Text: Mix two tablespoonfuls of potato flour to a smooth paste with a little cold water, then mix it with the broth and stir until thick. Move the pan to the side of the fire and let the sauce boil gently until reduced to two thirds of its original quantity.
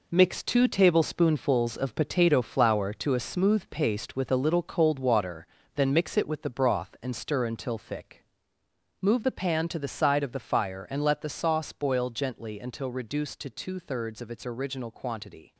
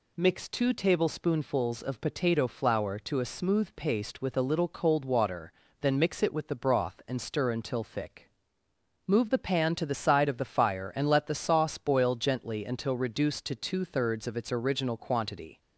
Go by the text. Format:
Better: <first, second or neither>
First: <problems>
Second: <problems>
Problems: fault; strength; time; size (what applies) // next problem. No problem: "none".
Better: second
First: gets quieter; strong; throughout; 9 dB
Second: none